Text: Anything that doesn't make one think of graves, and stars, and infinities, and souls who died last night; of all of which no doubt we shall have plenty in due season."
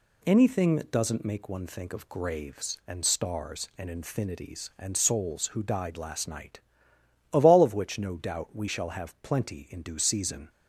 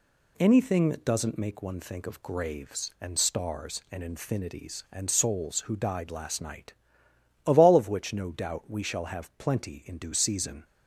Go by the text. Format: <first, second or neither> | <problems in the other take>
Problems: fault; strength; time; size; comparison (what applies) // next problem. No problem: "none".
neither | none